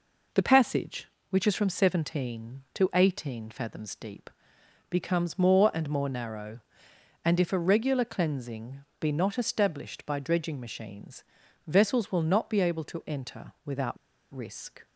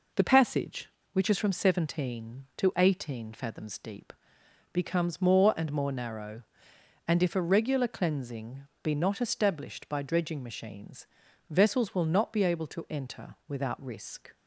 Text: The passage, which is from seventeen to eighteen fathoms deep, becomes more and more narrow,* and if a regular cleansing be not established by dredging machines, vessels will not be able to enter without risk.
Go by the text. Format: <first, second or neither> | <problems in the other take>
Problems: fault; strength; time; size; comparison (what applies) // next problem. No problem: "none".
second | pauses between "cleansing" and "be"; slight; at 8.7 s; 0.22 s long; slight in the second // pauses between "without" and "risk"; at 13.9 s; 0.36 s long